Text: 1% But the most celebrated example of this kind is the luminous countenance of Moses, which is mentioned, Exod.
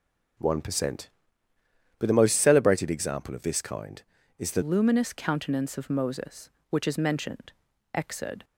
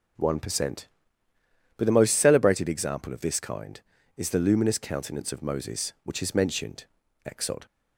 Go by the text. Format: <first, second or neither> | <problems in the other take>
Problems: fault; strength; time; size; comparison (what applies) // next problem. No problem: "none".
second | changes voice at "luminous"; from 4.6 s on; 3.8 s long